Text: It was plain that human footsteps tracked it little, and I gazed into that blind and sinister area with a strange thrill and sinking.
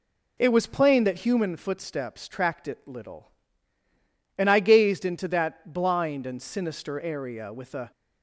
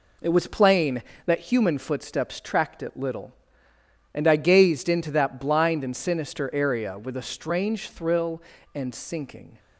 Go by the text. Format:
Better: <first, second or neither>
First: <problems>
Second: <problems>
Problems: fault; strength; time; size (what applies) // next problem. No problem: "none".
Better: second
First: stops before "strange thrill and sinking"; at 7.9 s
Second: none